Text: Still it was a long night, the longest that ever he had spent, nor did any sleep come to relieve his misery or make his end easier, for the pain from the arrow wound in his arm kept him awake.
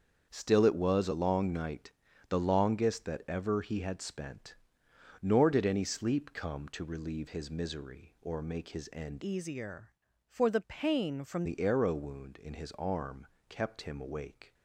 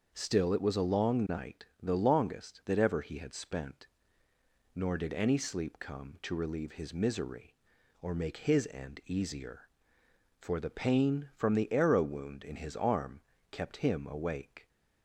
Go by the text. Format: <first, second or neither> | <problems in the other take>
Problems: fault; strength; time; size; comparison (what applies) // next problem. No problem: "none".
second | starts louder than the rest; until 1.3 s; 7 dB; also in the second // changes voice from "easier" to "from"; from 9.2 to 11.4 s; 2.2 s long // pauses between "arm" and "kept"; slight; at 13.2 s; 0.22 s long; slight in the second